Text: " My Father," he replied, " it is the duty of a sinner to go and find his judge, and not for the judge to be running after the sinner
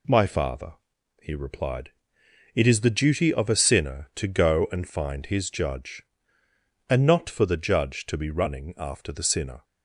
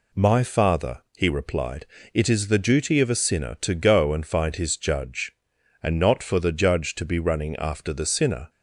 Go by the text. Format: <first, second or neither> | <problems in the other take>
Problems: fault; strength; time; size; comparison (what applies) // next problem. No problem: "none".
neither | none